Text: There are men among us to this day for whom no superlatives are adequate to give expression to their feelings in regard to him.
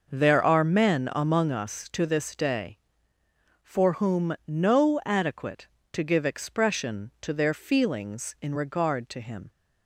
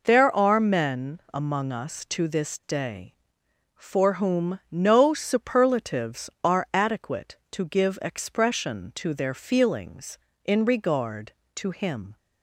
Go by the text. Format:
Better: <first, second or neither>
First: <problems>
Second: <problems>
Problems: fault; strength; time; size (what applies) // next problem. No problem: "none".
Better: second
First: skips "superlatives are"; at 5.0 s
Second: none